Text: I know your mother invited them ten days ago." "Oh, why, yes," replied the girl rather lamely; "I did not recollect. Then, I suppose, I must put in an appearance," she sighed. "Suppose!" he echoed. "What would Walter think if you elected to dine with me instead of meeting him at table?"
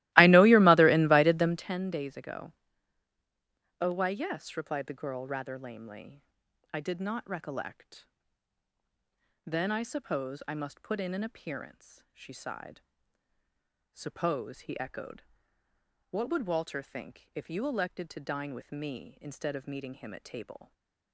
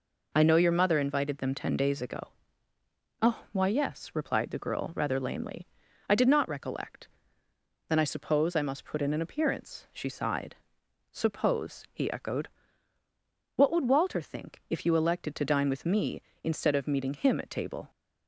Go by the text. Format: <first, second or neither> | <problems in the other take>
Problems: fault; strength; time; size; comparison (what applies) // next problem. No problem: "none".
second | starts louder than the rest; strong; until 1.7 s; 18 dB // stays silent after the last word; slight; from 20.6 s on; 0.5 s long